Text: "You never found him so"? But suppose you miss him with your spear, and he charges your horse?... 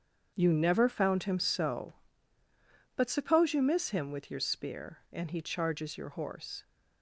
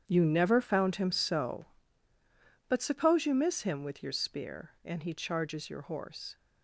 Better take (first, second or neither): first